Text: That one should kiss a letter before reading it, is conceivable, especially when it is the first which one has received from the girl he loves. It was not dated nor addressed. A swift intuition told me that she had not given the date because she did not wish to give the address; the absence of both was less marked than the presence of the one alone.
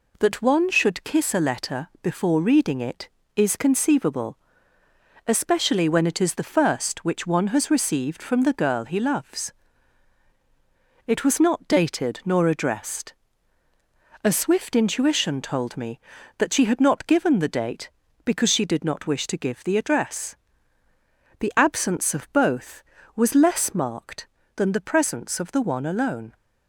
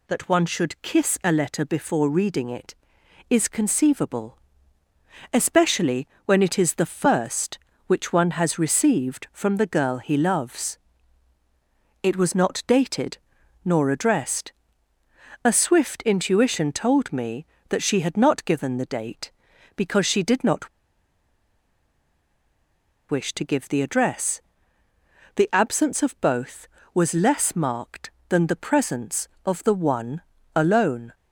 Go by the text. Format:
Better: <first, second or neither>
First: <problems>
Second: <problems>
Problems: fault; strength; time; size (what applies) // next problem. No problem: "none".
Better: first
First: none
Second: pauses between "especially" and "when"; slight; at 6.0 s; 0.20 s long // pauses between "dated" and "nor"; noticeable; at 13.1 s; 0.48 s long // pauses between "not" and "wish"; strong; at 20.6 s; 2.4 s long // pauses between "one" and "alone"; slight; at 30.2 s; 0.34 s long